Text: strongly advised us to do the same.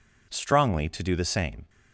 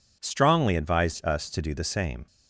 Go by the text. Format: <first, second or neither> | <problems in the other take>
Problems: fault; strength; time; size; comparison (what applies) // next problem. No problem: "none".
second | skips "advised us"; at 0.8 s